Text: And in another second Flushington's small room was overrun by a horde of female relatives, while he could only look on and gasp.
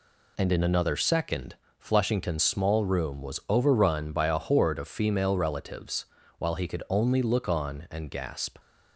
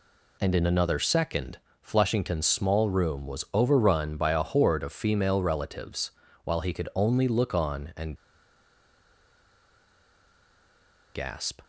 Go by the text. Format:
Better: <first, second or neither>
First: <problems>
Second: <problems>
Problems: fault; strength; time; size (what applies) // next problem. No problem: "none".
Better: first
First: pauses between "second" and "Flushington's"; slight; at 1.5 s; 0.24 s long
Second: pauses between "second" and "Flushington's"; slight; at 1.5 s; 0.24 s long // pauses between "and" and "gasp"; strong; at 8.1 s; 3.0 s long